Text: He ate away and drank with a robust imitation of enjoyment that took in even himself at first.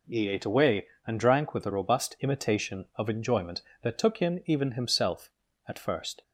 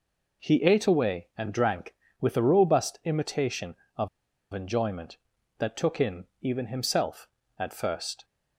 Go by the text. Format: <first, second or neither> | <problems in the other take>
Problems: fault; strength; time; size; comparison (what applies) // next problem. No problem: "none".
first | pauses between "of" and "enjoyment"; at 4.0 s; 0.44 s long